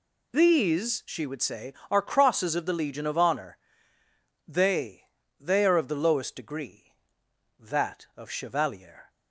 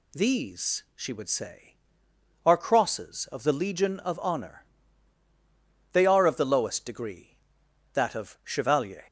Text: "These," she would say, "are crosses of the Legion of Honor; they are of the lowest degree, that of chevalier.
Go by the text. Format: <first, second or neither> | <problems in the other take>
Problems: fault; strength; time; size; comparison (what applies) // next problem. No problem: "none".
second | says "they" twice; at 5.3 s